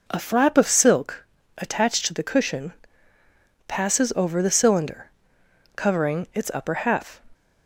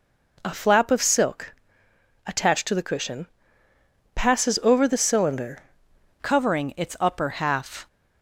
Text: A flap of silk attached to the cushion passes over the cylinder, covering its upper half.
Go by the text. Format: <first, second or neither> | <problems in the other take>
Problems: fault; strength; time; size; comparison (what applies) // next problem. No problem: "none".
first | pauses between "silk" and "attached"; noticeable; at 1.5 s; 0.72 s long; slight in the first // pauses between "cushion" and "passes"; noticeable; at 3.2 s; 0.88 s long; noticeable in the first // changes voice at "covering"; from 6.2 s on; 1.6 s long